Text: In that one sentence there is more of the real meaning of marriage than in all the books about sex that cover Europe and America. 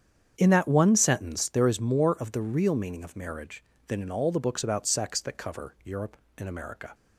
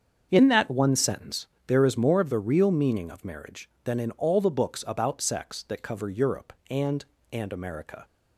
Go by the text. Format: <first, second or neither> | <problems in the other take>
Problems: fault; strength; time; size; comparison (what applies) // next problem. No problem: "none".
first | starts louder than the rest; until 1.3 s; 7 dB; strong in the first // pauses between "sentence" and "there"; slight; at 1.4 s; 0.18 s long // says "and" twice; at 7.3 s